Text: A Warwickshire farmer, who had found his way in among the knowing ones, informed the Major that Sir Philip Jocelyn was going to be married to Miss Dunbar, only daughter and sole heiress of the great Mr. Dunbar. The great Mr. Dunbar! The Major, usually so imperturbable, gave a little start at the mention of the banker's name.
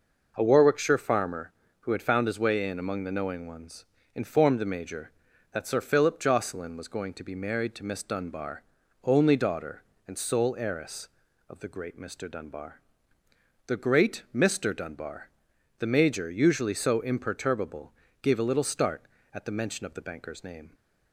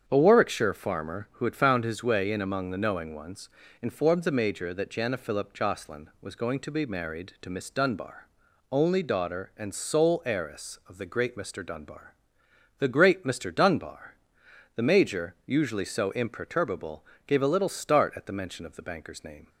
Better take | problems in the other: first | starts louder than the rest; strong; until 1.0 s; 8 dB // says "Jana" for "Sir"; at 4.9 s

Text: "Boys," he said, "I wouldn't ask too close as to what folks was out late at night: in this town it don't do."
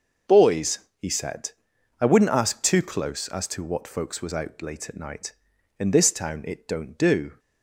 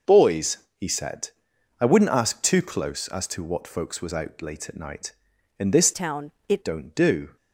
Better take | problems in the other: first | changes voice from "town" to "it"; from 5.9 to 6.6 s; 0.7 s long // pauses between "town" and "it"; slight; at 6.3 s; 0.18 s long

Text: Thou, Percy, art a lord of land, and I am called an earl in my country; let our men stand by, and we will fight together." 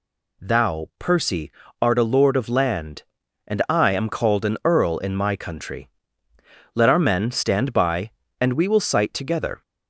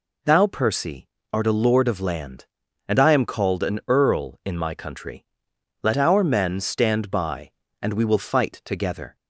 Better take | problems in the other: second | says "sight" for "fight"; at 8.8 s

